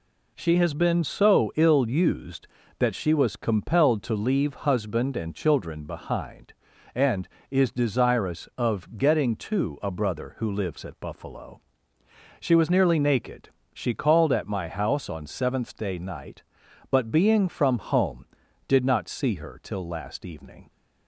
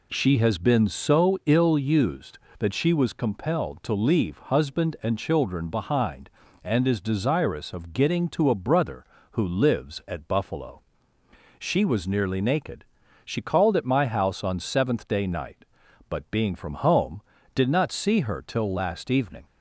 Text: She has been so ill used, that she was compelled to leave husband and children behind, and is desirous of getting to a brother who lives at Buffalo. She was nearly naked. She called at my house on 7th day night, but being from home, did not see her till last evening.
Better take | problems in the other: neither | none

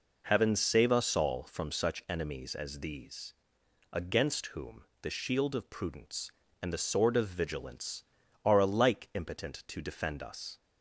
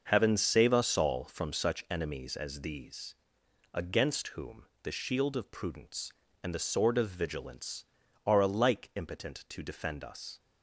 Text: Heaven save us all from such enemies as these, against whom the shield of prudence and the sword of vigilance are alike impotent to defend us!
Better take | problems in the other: first | gets quieter; strong; throughout; 9 dB // pauses between "whom" and "the"; slight; at 4.6 s; 0.18 s long; slight in the first

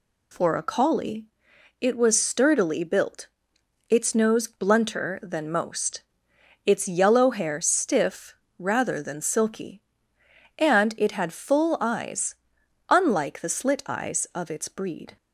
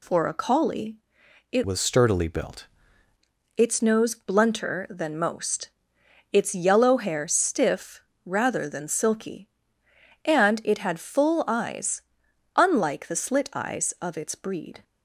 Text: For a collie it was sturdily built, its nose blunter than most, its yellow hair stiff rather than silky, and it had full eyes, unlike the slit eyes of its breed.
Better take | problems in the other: first | pauses between "collie" and "it"; noticeable; at 0.9 s; 0.56 s long; noticeable in the first // changes voice from "was" to "built"; from 1.6 to 2.6 s; 1.0 s long // pauses between "stiff" and "rather"; slight; at 7.9 s; 0.24 s long; slight in the first

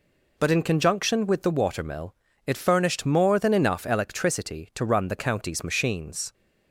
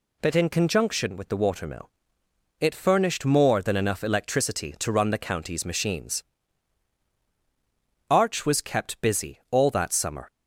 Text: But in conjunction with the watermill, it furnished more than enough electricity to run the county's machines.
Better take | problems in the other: first | goes on to say "Arch was kept busy all that summer"; strong; from 8.0 s on; 2.2 s long

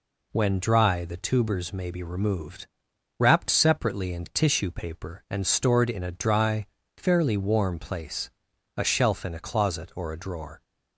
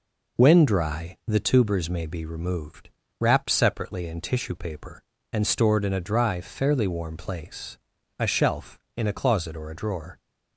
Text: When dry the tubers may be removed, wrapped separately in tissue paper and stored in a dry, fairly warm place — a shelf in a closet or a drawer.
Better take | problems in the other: neither | none

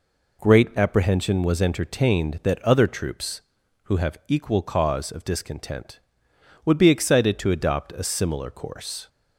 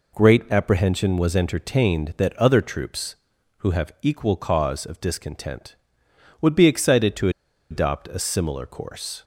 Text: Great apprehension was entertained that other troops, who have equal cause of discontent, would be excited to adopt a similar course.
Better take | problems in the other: first | pauses between "to" and "adopt"; at 7.2 s; 0.41 s long

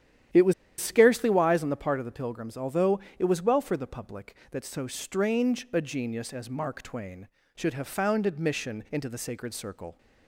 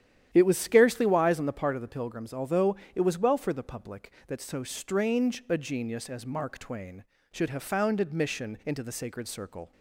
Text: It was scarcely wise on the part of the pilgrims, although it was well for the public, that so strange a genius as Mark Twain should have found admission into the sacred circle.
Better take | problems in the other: second | starts louder than the rest; strong; until 1.6 s; 10.5 dB; strong in the second // pauses between "was" and "scarcely"; slight; at 0.5 s; 0.25 s long // pauses between "although" and "it"; slight; at 2.9 s; 0.18 s long; slight in the second

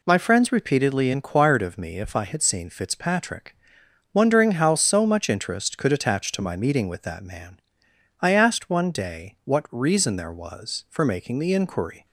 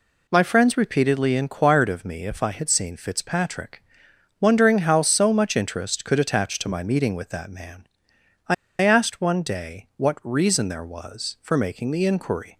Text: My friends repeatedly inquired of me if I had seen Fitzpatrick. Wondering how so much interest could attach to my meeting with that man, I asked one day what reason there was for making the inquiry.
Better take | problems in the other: first | pauses between "I" and "asked"; slight; at 8.5 s; 0.26 s long

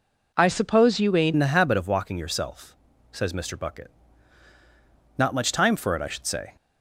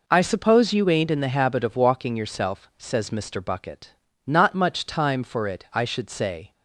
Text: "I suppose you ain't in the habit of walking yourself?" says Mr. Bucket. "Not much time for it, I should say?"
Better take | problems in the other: second | changes voice at "in"; from 1.3 s on; 5.2 s long

